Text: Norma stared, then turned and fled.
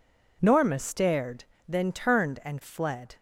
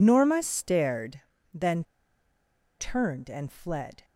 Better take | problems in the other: first | pauses between "then" and "turned"; noticeable; at 1.8 s; 0.95 s long

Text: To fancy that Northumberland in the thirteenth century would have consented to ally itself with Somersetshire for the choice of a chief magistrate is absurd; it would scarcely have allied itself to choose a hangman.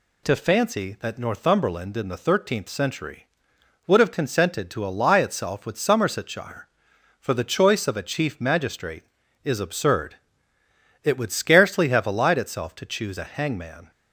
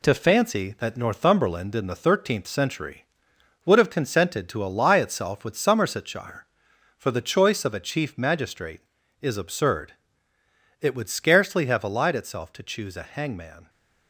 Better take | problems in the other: first | gets quieter; noticeable; throughout; 5 dB

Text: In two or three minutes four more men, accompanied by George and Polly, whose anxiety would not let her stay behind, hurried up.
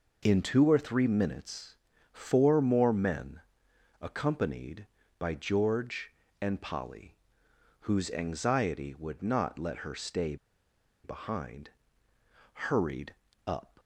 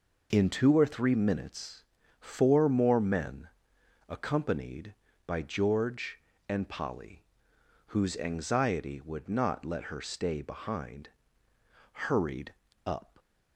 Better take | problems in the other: second | pauses between "minutes" and "four"; at 1.7 s; 0.38 s long; also in the second // pauses between "stay" and "behind"; noticeable; at 10.3 s; 0.68 s long // pauses between "hurried" and "up"; slight; at 13.1 s; 0.32 s long; slight in the second

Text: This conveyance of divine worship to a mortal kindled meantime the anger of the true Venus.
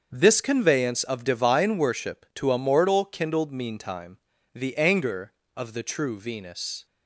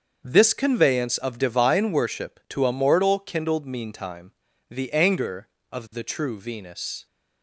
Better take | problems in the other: neither | starts louder than the rest; the same in both // pauses between "meantime" and "the"; the same in both

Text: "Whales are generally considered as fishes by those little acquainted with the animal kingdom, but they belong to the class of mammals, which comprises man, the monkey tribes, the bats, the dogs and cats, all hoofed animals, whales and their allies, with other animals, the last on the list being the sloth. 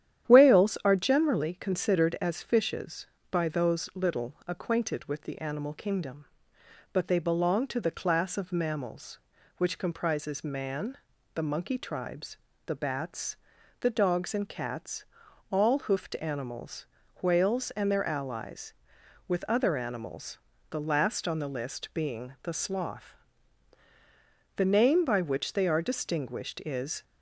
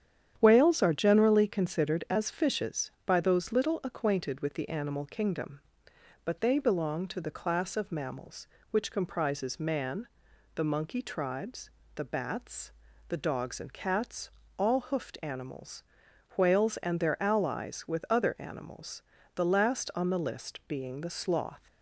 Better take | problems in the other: second | starts louder than the rest; strong; until 1.3 s; 10.5 dB; strong in the second // goes on to say "The name by which they are distinguished is"; strong; from 24.5 s on; 2.4 s long

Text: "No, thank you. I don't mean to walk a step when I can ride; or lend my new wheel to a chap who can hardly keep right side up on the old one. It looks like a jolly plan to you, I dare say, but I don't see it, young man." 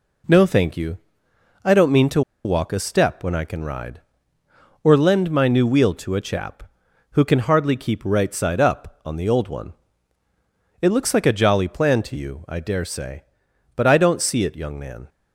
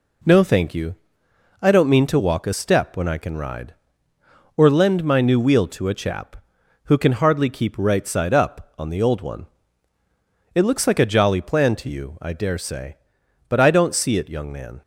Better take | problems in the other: second | pauses between "to" and "walk"; slight; at 2.2 s; 0.23 s long

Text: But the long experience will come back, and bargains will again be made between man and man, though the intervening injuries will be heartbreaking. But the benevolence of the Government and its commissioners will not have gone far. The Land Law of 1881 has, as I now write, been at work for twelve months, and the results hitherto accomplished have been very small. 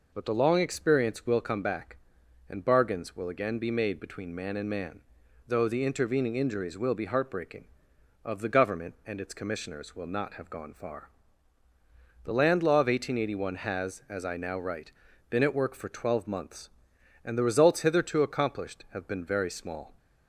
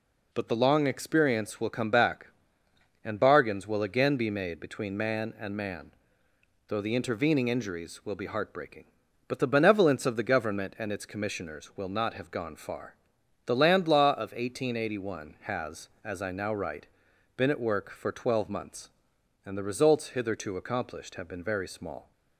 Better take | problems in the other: second | skips "But the benevolence"; at 7.9 s

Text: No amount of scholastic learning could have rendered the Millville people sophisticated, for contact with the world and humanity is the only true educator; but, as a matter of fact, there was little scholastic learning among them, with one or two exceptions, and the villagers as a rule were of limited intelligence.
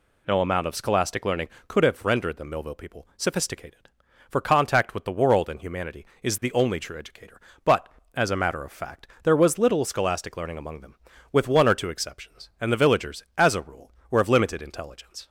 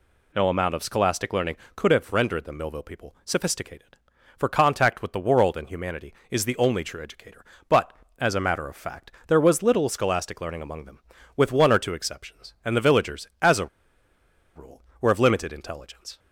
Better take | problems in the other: first | pauses between "a" and "rule"; noticeable; at 13.6 s; 0.89 s long

